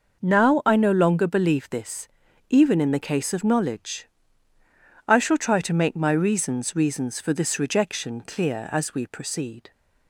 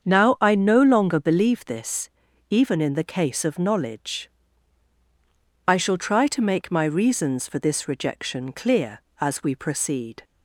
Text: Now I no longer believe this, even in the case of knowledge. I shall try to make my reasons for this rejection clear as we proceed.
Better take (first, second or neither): second